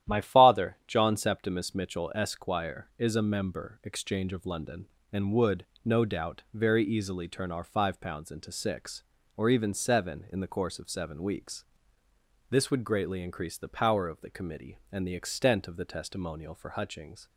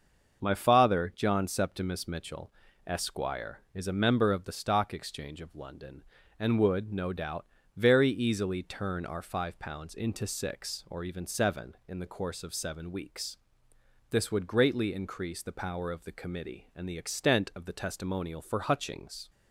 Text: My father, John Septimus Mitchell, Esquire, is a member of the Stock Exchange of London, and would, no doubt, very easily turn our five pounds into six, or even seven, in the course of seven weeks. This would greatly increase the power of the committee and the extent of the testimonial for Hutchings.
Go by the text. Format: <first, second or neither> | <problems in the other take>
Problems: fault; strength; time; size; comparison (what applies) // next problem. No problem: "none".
second | starts louder than the rest; strong; until 1.1 s; 11.5 dB; also in the second // skips "of the Stock"; at 3.8 s